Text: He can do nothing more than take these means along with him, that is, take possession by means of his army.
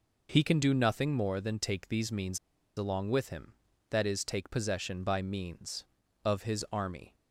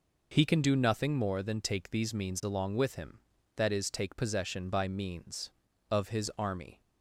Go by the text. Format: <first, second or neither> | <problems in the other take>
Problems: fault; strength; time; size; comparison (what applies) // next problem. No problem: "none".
second | pauses between "means" and "along"; at 2.3 s; 0.38 s long